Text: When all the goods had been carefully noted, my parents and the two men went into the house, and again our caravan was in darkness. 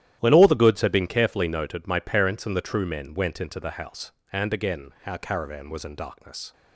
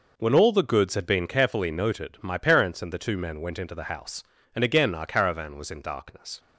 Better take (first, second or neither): second